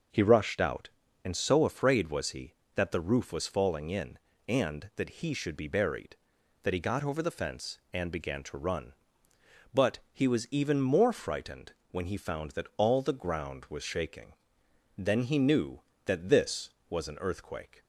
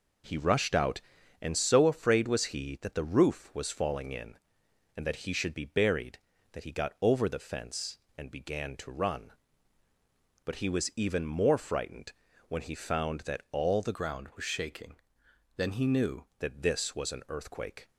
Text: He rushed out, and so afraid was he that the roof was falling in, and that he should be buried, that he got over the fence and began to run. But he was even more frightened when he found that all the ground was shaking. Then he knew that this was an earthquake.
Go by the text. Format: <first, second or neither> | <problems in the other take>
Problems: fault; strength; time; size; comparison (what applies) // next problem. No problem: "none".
first | pauses between "frightened" and "when"; slight; at 12.1 s; 0.36 s long; slight in the first // changes voice from "ground" to "knew"; from 13.9 to 16.2 s; 2.3 s long